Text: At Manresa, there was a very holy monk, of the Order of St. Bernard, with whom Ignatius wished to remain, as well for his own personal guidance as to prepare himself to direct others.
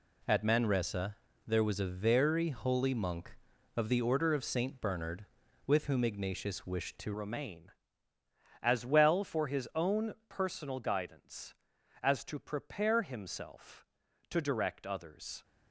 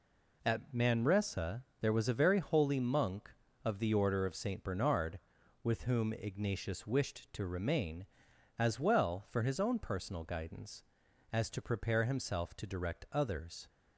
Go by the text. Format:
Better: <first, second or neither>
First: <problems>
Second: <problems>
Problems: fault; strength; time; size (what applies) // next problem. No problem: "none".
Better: second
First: changes voice at "remain"; from 7.1 s on; 8.3 s long // pauses between "own" and "personal"; slight; at 10.1 s; 0.16 s long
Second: none